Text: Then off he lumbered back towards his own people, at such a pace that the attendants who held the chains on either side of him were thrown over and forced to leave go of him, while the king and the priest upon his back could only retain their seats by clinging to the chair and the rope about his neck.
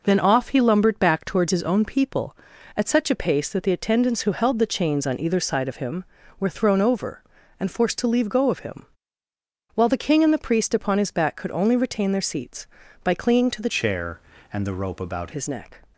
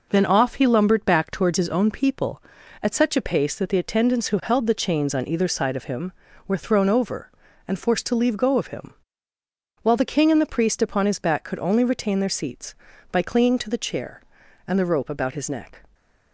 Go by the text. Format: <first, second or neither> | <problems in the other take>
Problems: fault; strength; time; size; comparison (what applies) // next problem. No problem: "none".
second | changes voice from "chair" to "about"; from 13.6 to 15.3 s; 1.7 s long